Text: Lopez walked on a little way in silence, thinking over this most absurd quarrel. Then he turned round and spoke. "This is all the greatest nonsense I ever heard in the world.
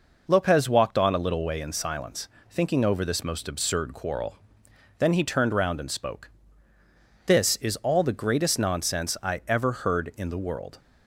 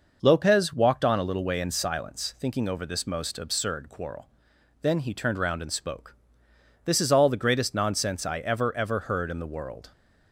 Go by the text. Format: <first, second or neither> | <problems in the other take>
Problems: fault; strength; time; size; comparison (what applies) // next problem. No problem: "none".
first | says "ever" twice; at 8.7 s